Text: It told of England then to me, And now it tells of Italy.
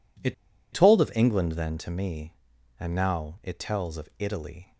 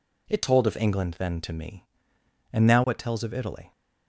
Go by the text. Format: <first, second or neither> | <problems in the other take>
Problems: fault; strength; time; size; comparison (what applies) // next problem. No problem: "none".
second | pauses between "It" and "told"; at 0.3 s; 0.38 s long